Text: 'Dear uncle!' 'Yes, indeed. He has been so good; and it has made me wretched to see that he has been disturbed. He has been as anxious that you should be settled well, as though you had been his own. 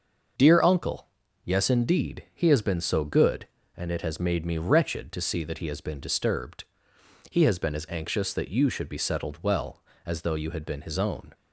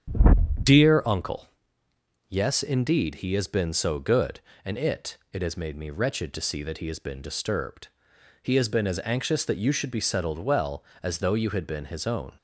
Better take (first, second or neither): first